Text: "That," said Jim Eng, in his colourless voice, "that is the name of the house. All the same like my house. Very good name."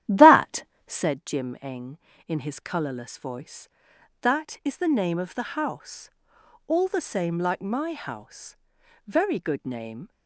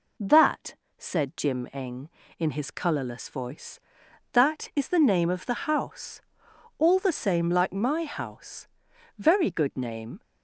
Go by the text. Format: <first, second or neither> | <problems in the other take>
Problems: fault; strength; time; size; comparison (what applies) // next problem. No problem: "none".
second | starts louder than the rest; strong; until 1.2 s; 12 dB